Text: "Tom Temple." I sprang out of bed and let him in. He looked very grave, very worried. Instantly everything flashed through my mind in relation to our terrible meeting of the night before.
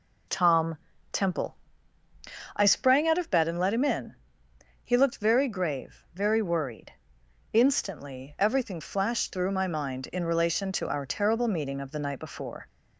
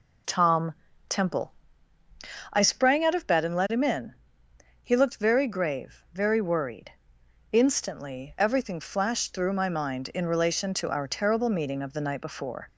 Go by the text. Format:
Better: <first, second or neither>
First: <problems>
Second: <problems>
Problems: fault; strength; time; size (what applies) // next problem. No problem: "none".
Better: neither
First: pauses between "Tom" and "Temple"; slight; at 0.7 s; 0.34 s long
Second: pauses between "Tom" and "Temple"; slight; at 0.7 s; 0.34 s long